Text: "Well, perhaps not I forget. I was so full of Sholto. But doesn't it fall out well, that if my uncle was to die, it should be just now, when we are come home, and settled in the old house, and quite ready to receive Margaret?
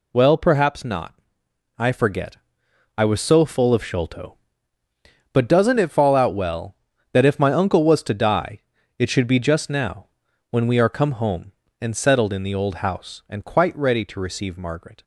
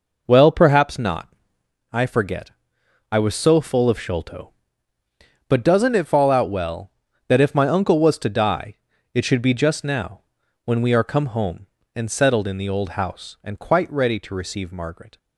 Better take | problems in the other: first | starts louder than the rest; noticeable; until 1.7 s; 5 dB // pauses between "not" and "I"; noticeable; at 1.2 s; 0.62 s long; noticeable in the first

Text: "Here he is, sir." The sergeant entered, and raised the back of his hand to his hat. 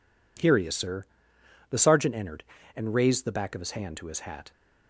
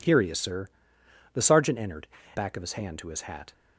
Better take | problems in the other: first | skips "and raised the"; at 2.2 s

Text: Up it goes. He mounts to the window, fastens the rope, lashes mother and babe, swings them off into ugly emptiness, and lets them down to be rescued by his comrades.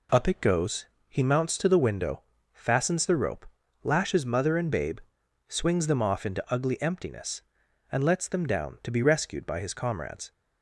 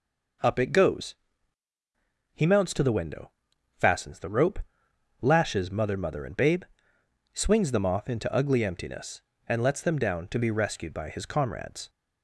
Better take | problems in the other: first | says "mother" twice; at 5.9 s

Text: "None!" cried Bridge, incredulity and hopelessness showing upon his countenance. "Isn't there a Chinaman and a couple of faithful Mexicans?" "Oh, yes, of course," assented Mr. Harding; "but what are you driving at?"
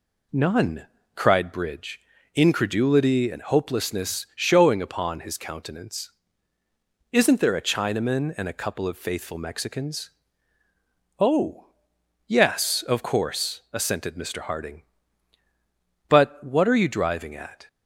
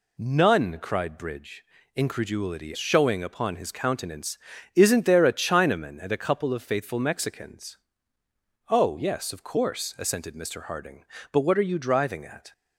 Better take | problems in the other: first | skips "and hopelessness"; at 2.7 s

